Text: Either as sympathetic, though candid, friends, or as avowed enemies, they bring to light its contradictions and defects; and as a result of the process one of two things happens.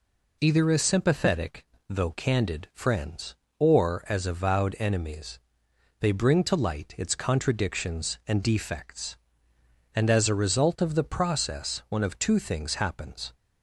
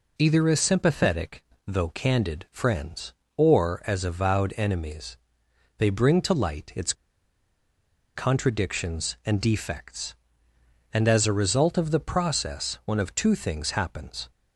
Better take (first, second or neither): first